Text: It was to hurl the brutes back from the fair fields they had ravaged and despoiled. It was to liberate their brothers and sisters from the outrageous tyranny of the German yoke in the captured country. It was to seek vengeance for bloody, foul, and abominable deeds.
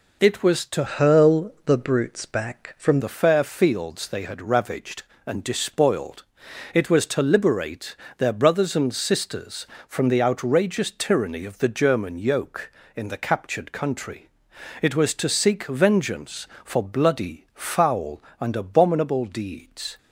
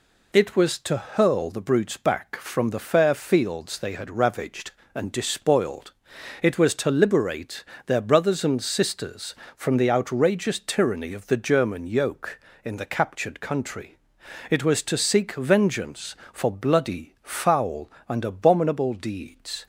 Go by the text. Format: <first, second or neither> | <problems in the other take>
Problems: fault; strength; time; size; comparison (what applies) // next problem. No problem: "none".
second | changes voice from "hurl" to "from"; from 0.8 to 2.9 s; 2.1 s long // pauses between "liberate" and "their"; slight; at 7.9 s; 0.22 s long; slight in the second